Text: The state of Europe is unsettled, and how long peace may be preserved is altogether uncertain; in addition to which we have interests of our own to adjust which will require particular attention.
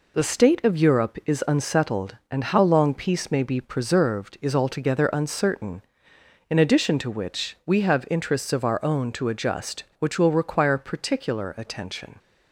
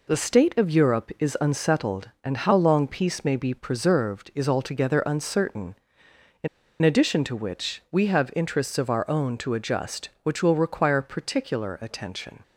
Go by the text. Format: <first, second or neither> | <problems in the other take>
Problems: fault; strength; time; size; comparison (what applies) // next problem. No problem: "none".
first | pauses between "in" and "addition"; slight; at 6.4 s; 0.34 s long